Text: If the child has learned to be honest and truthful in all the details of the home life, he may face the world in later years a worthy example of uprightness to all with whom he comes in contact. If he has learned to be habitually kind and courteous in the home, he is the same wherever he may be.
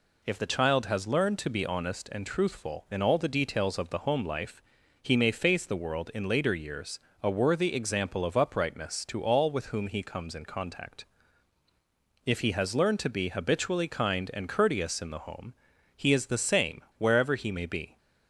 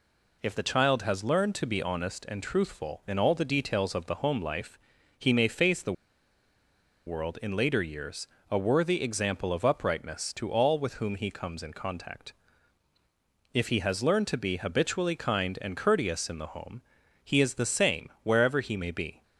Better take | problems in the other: first | pauses between "the" and "world"; at 5.9 s; 1.1 s long // pauses between "years" and "a"; slight; at 8.2 s; 0.22 s long; slight in the first

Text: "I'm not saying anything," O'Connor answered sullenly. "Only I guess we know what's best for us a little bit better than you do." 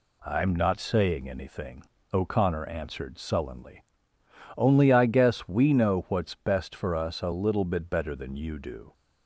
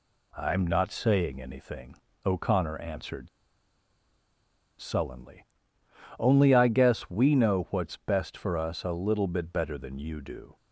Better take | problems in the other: first | pauses between "answered" and "sullenly"; strong; at 3.2 s; 1.5 s long

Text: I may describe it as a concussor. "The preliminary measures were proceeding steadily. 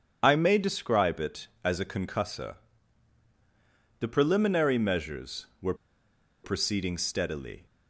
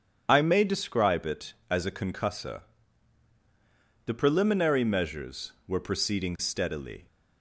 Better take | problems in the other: second | pauses between "were" and "proceeding"; noticeable; at 5.7 s; 0.68 s long

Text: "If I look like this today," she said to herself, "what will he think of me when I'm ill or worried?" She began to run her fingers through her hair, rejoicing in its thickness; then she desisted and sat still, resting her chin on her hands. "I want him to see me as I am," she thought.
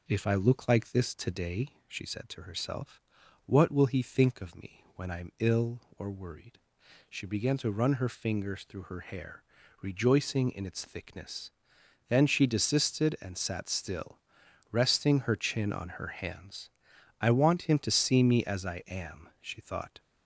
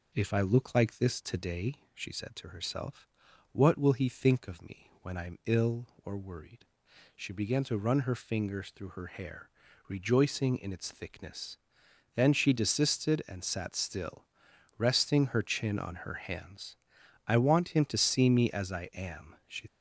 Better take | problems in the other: first | stops before "thought"; at 19.6 s

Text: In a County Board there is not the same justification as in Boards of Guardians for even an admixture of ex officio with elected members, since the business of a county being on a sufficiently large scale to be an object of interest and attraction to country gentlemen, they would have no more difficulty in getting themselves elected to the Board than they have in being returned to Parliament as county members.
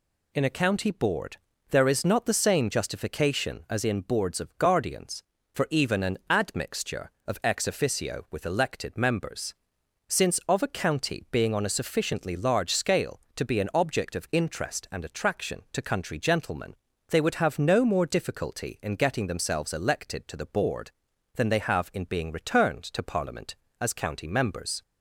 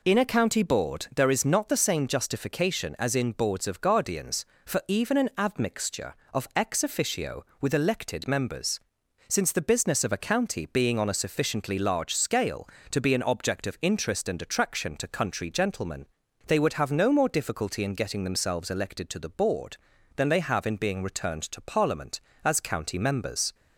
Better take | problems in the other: second | pauses between "Board" and "there"; slight; at 1.3 s; 0.36 s long // skips "the business"; at 10.4 s

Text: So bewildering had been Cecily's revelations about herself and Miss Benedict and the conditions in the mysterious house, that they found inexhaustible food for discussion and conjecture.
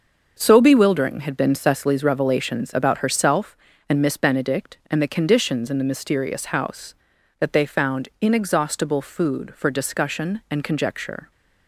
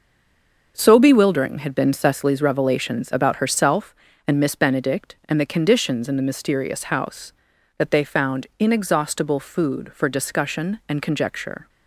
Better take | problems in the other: first | stays silent before the first word; slight; until 0.7 s; 0.7 s long // starts louder than the rest; noticeable; until 1.7 s; 6 dB; noticeable in the first

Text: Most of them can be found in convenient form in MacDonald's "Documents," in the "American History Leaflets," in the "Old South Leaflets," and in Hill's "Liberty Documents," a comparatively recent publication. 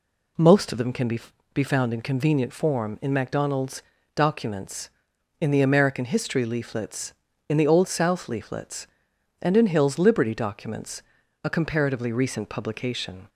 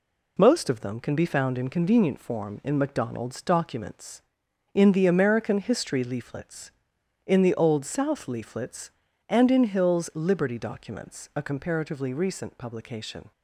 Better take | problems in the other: second | says "be" twice; at 1.5 s // pauses between "MacDonald's" and "Documents"; slight; at 3.8 s; 0.32 s long

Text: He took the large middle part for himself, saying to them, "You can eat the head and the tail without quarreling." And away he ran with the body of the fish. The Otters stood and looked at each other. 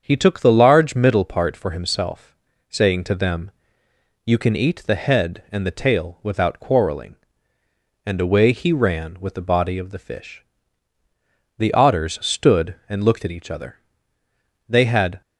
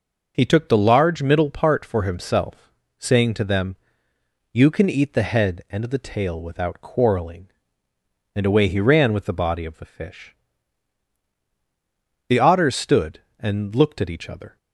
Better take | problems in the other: second | starts louder than the rest; strong; until 1.0 s; 7 dB // goes on to say "They had"; from 14.6 s on; 0.54 s long

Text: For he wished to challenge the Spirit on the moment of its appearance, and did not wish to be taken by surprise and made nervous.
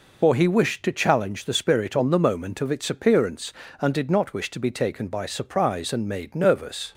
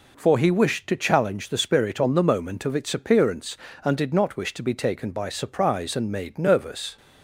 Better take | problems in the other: second | loses the start of "For"; at 0.2 s; 100 ms

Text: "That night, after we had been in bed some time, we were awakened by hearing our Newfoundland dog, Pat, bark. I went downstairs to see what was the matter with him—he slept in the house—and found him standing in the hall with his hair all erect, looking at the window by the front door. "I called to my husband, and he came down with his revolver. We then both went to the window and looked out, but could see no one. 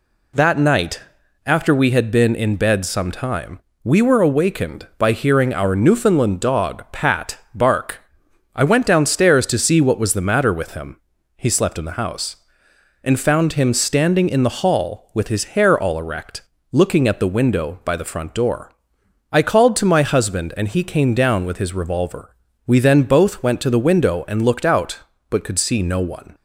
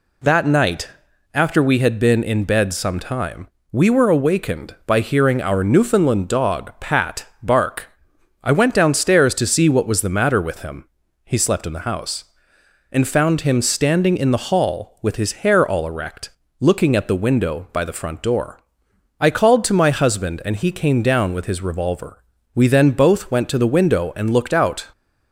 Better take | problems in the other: first | stops before "but could see no one"; at 24.9 s

